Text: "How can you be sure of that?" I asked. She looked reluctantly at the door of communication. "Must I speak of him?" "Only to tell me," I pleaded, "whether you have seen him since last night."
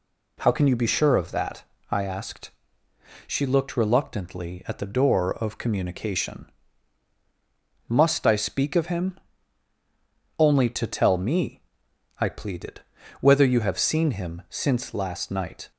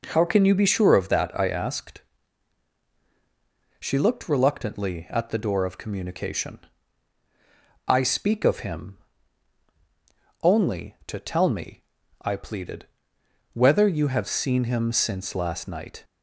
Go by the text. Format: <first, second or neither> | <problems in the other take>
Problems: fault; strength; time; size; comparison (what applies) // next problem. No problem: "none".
first | skips "Must"; at 7.2 s